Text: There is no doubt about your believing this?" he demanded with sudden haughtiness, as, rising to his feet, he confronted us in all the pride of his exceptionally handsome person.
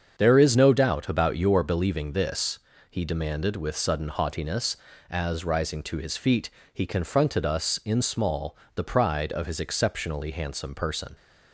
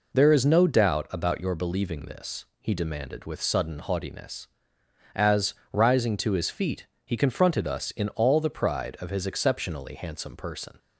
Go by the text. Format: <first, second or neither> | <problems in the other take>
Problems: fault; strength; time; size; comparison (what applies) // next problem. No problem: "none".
second | starts louder than the rest; strong; until 1.2 s; 7 dB // says "small" for "all"; at 8.0 s